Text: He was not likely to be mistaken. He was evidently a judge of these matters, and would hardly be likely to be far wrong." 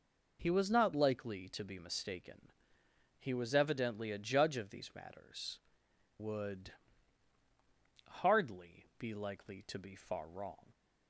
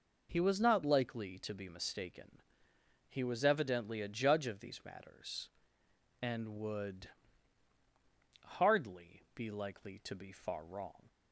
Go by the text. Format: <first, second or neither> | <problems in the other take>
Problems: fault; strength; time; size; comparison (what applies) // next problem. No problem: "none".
second | skips "and"; at 5.9 s // pauses between "would" and "hardly"; strong; at 6.7 s; 1.3 s long; strong in the second